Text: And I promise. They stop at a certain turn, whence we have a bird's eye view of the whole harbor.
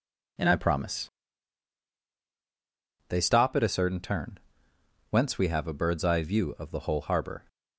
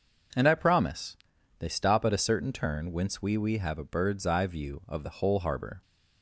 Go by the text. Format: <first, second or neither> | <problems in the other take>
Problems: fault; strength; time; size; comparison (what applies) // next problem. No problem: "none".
first | says "we" twice; at 3.3 s